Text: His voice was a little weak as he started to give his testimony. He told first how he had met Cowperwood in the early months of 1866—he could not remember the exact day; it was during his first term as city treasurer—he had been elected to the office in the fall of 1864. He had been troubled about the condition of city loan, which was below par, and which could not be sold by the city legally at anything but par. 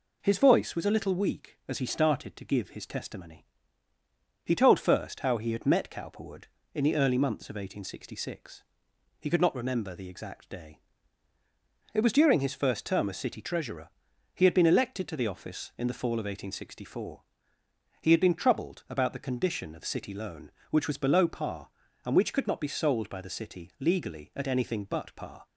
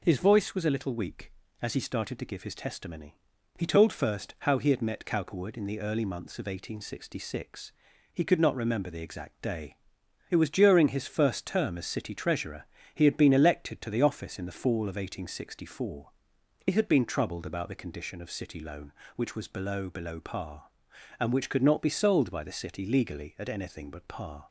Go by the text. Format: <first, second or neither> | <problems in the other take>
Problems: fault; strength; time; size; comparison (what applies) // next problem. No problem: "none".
first | says "below" twice; at 19.8 s